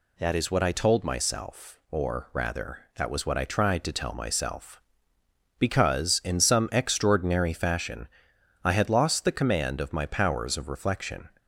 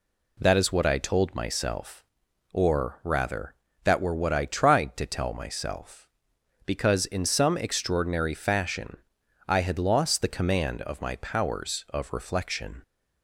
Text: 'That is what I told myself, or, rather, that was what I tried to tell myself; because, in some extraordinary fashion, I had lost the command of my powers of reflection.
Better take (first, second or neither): first